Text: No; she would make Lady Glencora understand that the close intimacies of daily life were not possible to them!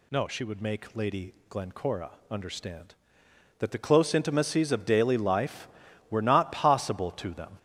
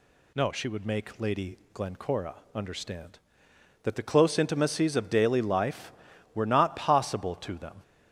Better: second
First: gets louder; throughout; 7 dB // pauses between "Lady" and "Glencora"; slight; at 1.3 s; 0.16 s long // pauses between "Glencora" and "understand"; slight; at 2.1 s; 0.20 s long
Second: pauses between "Lady" and "Glencora"; slight; at 1.5 s; 0.16 s long // pauses between "Glencora" and "understand"; slight; at 2.3 s; 0.20 s long

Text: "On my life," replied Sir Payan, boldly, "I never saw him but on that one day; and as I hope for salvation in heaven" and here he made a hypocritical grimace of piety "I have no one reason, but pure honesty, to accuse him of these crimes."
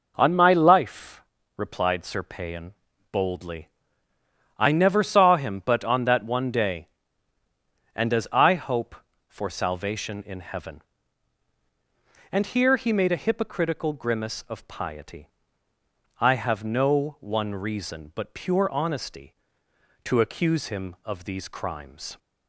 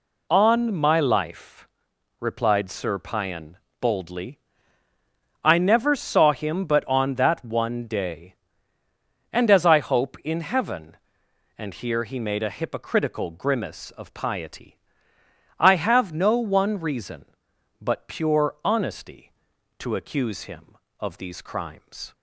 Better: first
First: pauses between "piety" and "I"; noticeable; at 15.3 s; 0.90 s long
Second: skips "for salvation"; at 10.2 s // pauses between "piety" and "I"; noticeable; at 14.7 s; 0.82 s long

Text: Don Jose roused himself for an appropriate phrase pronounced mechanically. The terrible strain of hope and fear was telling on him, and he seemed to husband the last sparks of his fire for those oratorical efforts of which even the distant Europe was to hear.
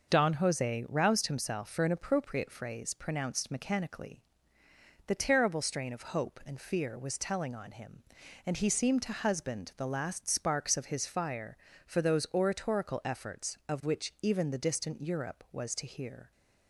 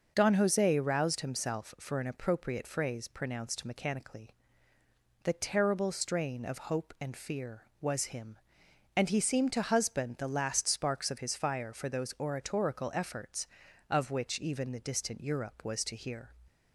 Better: first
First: none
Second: skips "telling on"; at 8.0 s

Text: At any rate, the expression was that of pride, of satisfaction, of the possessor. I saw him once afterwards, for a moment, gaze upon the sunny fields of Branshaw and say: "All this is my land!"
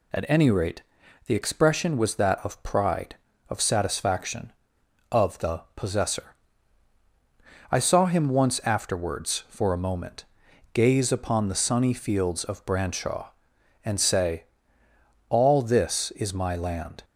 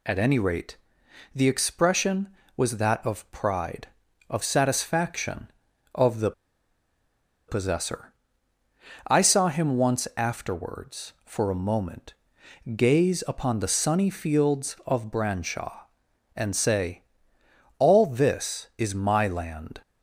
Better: first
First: none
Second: pauses between "the" and "possessor"; at 6.3 s; 1.1 s long

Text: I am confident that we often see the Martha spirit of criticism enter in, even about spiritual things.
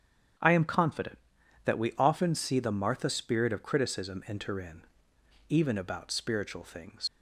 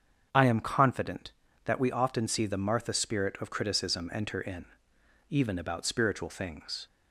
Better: second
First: starts louder than the rest; strong; until 1.8 s; 8.5 dB // leaves "things" unfinished; at 7.0 s; 95 ms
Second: starts louder than the rest; strong; until 1.3 s; 7 dB

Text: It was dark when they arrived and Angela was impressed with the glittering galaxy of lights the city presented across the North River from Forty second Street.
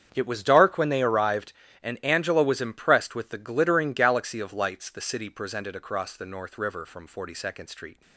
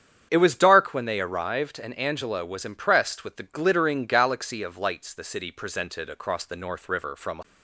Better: first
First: starts louder than the rest; strong; until 1.1 s; 7.5 dB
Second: starts louder than the rest; strong; until 1.3 s; 8.5 dB // stops before "Forty second Street"; at 7.4 s

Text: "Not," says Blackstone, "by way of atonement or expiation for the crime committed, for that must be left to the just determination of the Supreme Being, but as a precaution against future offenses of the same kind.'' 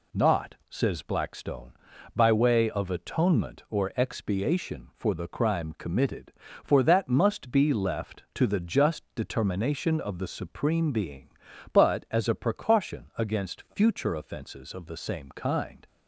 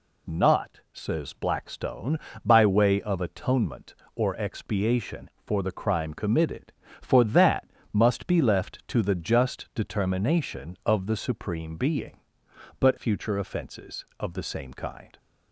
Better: first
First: none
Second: pauses between "that" and "must"; slight; at 7.6 s; 0.24 s long // skips "as a precaution against"; at 12.9 s

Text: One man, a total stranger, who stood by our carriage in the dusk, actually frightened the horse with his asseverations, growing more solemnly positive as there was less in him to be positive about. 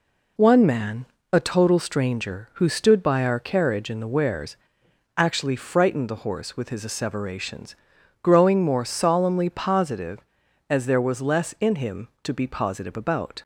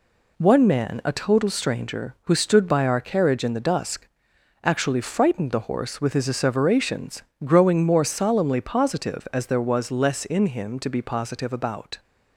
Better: second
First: says "wares" for "dusk"; at 4.1 s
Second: none

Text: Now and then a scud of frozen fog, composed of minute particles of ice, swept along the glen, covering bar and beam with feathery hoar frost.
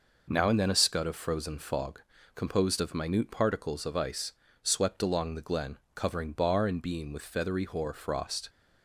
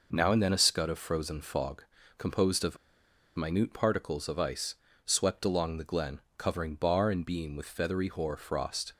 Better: first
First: none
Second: pauses between "of" and "minute"; noticeable; at 2.7 s; 0.59 s long

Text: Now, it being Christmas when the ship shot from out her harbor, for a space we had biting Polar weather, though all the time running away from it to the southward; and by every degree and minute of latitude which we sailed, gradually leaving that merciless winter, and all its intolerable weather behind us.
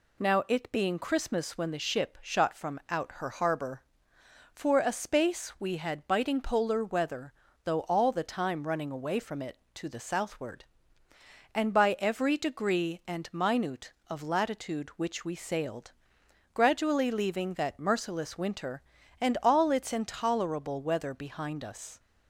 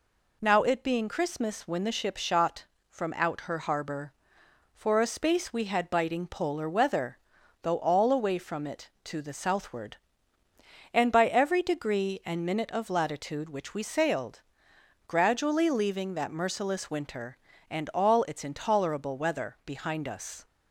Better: first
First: none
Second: skips "the time running"; at 8.1 s

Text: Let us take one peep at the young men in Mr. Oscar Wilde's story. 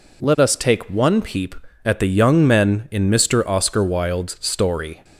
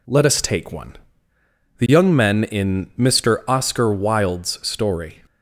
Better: first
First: none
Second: skips "peep at"; at 1.3 s

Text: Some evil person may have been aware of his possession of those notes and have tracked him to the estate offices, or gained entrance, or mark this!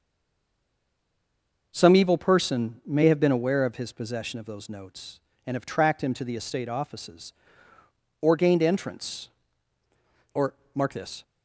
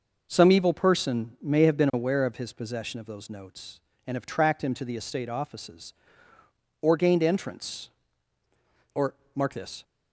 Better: second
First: stays silent before the first word; noticeable; until 1.7 s; 1.7 s long // pauses between "or" and "mark"; slight; at 10.5 s; 0.22 s long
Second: pauses between "or" and "mark"; slight; at 9.1 s; 0.22 s long

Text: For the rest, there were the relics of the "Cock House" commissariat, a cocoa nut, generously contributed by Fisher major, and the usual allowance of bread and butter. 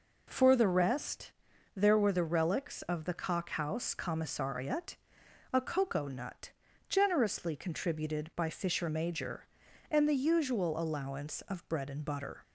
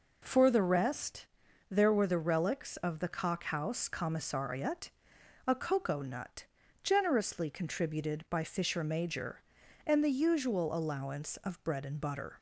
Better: neither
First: none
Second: none

